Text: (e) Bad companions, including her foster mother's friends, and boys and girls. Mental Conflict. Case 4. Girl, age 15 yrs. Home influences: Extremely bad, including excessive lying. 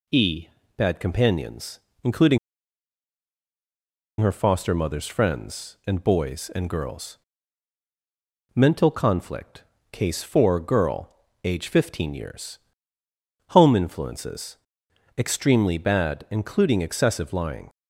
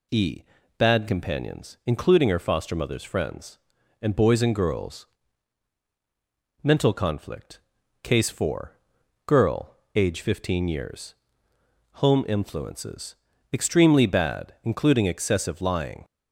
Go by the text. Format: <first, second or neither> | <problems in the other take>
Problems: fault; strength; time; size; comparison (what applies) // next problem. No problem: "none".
second | pauses between "including" and "her"; strong; at 2.3 s; 1.8 s long